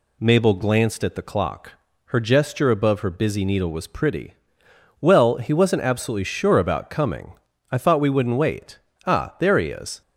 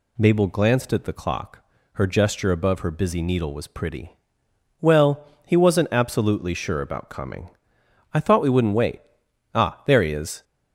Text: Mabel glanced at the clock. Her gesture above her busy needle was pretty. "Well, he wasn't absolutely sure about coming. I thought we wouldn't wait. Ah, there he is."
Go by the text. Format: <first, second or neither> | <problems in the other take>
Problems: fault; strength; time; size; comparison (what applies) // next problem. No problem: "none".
neither | none